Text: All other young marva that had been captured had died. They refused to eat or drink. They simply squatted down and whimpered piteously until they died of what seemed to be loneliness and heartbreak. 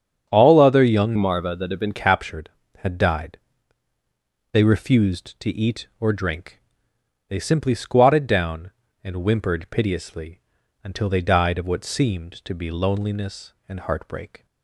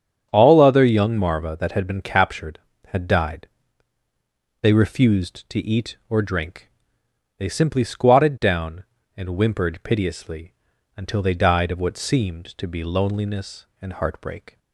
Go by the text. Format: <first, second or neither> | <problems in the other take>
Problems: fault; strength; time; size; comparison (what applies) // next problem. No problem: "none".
second | starts louder than the rest; strong; until 1.3 s; 8.5 dB; strong in the second // changes voice from "marva" to "been"; from 1.1 to 1.9 s; 0.8 s long // pauses between "piteously" and "until"; at 10.4 s; 0.42 s long; also in the second